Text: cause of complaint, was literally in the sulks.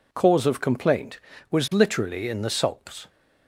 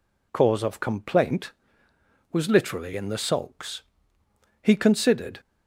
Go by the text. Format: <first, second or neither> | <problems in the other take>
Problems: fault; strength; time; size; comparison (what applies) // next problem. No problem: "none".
first | goes on to say "He considered"; noticeable; from 4.6 s on; 0.78 s long